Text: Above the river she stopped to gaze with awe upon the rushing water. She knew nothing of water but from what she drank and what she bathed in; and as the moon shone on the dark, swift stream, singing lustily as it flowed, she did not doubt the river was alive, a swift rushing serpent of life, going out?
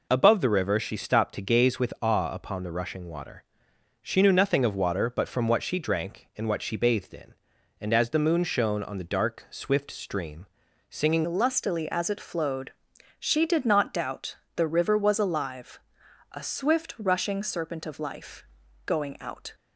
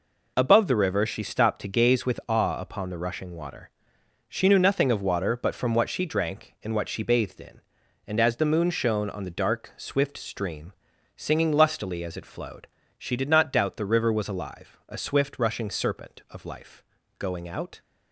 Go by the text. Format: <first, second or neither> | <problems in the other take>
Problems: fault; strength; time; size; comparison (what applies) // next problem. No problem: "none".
second | changes voice at "lustily"; from 11.2 s on; 8.3 s long // pauses between "doubt" and "the"; slight; at 14.3 s; 0.20 s long